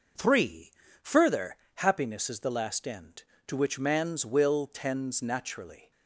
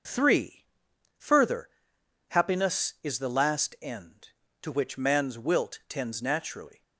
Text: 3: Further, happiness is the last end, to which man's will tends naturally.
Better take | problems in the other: first | says "wilt" for "will"; at 5.3 s

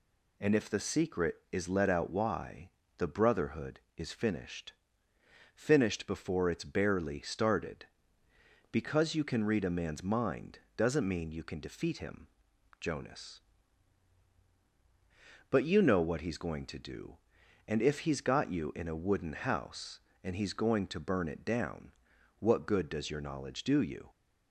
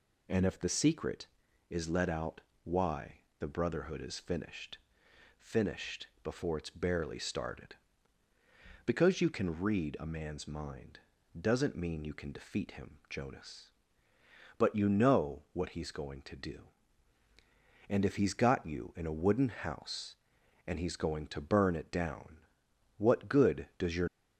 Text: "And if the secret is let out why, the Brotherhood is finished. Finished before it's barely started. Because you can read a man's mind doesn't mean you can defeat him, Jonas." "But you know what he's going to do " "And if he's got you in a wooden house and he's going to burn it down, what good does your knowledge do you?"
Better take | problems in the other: first | pauses between "out" and "why"; slight; at 2.4 s; 0.22 s long // pauses between "Finished" and "before"; slight; at 6.0 s; 0.16 s long // pauses between "mind" and "doesn't"; at 11.0 s; 0.38 s long; slight in the first // stops before "knowledge do you"; at 24.0 s

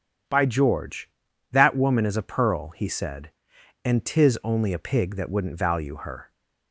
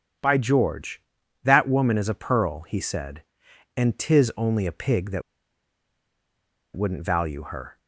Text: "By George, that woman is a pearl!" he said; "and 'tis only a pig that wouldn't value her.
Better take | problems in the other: first | starts louder than the rest; strong; until 1.6 s; 8 dB // pauses between "that" and "wouldn't"; strong; at 5.2 s; 1.5 s long

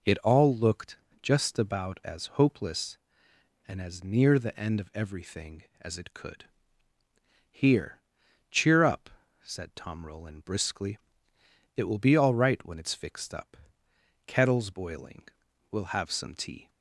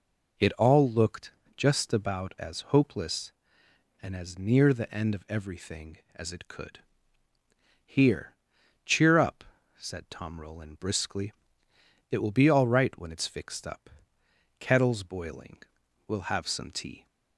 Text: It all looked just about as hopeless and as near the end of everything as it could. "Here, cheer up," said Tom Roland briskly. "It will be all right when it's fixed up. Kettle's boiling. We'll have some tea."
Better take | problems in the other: neither | pauses between "looked" and "just"; slight; the same in both

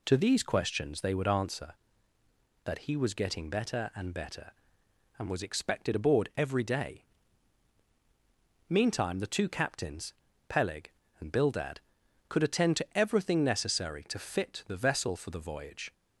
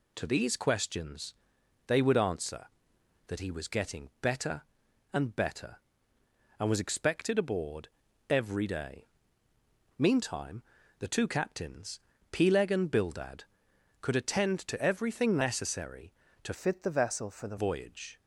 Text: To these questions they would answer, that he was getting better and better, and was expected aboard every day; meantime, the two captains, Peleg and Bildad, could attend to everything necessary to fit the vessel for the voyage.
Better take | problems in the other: first | pauses between "questions" and "they"; noticeable; at 1.3 s; 0.52 s long // pauses between "aboard" and "every"; at 7.8 s; 0.40 s long // changes voice from "fit" to "the"; from 16.5 to 17.5 s; 1.0 s long

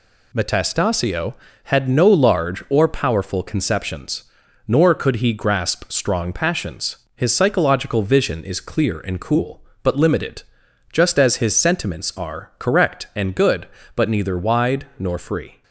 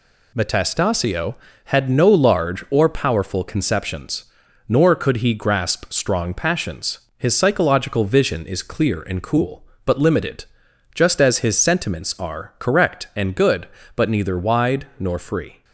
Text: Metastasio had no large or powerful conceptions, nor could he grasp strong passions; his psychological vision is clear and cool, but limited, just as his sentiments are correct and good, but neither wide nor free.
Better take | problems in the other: neither | none

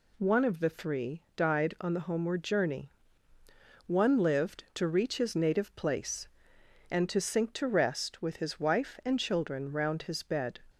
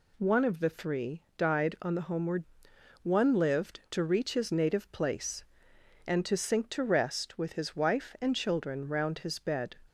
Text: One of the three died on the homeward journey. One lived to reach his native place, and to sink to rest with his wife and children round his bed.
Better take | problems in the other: first | skips "journey"; at 2.7 s

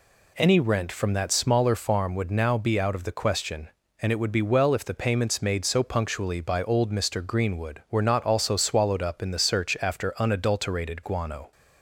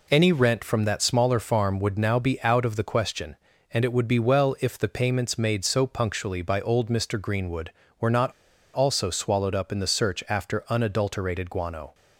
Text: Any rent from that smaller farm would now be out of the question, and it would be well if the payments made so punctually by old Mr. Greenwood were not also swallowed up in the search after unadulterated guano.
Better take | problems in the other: first | pauses between "not" and "also"; at 8.3 s; 0.42 s long

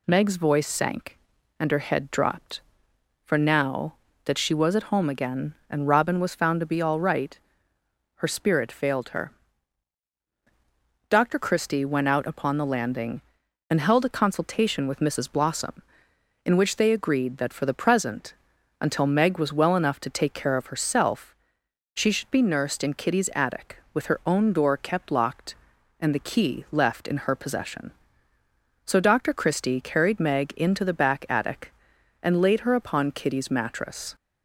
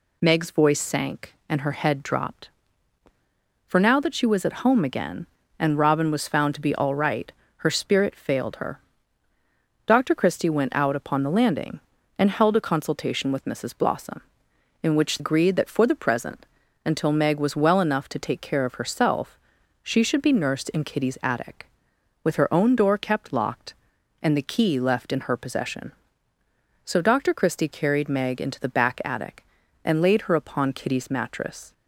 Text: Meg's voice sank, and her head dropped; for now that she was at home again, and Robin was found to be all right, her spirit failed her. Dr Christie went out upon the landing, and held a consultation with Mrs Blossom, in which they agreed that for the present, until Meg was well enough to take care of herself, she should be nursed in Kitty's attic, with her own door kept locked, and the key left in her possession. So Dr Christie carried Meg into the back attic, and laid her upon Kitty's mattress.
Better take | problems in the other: first | skips "they"; at 15.1 s

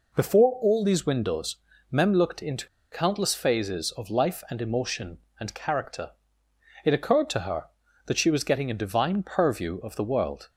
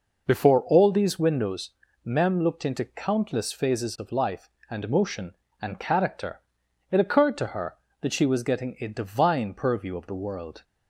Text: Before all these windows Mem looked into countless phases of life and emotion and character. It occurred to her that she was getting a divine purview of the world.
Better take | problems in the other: second | pauses between "windows" and "Mem"; slight; at 1.5 s; 0.34 s long; slight in the second // pauses between "into" and "countless"; slight; at 2.6 s; 0.25 s long

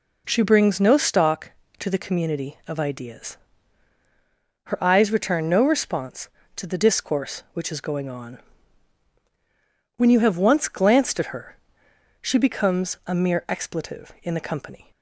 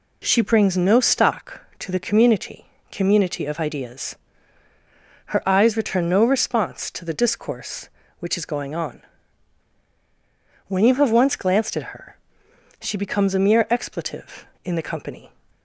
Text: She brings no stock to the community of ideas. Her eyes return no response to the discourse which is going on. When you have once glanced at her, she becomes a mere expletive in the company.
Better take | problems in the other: first | says "community" twice; at 2.9 s

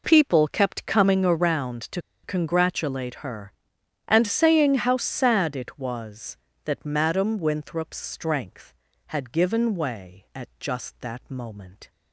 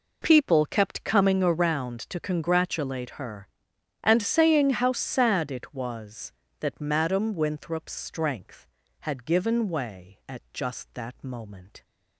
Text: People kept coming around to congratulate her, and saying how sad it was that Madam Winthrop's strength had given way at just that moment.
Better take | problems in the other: second | pauses between "to" and "congratulate"; slight; at 1.9 s; 0.24 s long

